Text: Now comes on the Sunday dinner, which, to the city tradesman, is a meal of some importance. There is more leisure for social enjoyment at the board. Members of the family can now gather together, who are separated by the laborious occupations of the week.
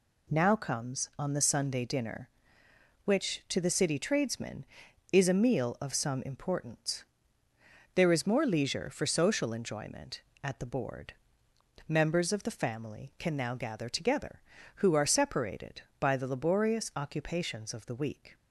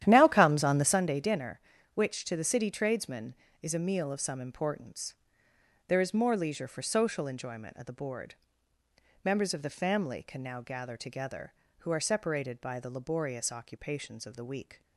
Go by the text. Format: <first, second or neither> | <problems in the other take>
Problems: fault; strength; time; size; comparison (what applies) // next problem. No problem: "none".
first | starts louder than the rest; strong; until 1.1 s; 11 dB